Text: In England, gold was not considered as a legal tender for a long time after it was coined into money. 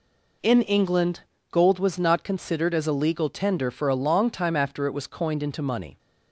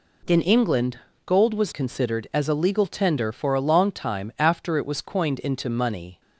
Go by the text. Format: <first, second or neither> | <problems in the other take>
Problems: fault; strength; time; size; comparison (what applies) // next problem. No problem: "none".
first | skips "not"; at 1.7 s